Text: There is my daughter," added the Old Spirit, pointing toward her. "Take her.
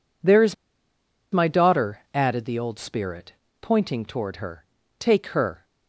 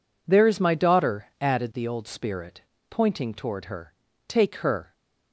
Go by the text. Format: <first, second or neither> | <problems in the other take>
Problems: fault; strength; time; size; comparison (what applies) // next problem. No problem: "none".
second | pauses between "is" and "my"; noticeable; at 0.5 s; 0.77 s long